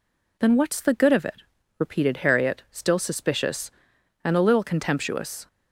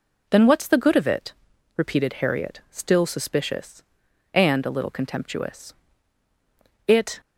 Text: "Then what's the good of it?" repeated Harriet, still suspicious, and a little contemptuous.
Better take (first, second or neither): first